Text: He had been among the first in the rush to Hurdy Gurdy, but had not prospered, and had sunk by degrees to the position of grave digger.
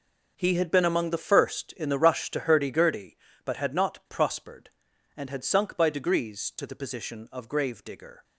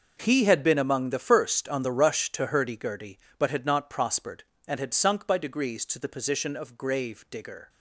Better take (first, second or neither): first